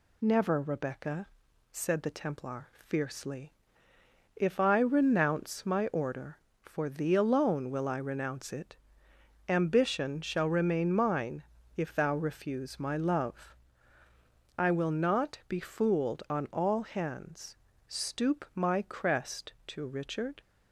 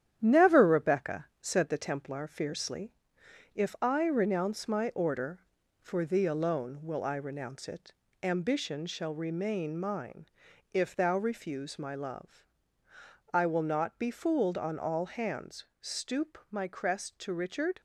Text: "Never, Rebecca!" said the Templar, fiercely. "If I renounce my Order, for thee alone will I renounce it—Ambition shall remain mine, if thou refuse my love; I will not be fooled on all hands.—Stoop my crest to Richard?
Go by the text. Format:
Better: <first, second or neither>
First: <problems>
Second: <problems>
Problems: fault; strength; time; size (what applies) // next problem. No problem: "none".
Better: first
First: none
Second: gets quieter; noticeable; throughout; 5.5 dB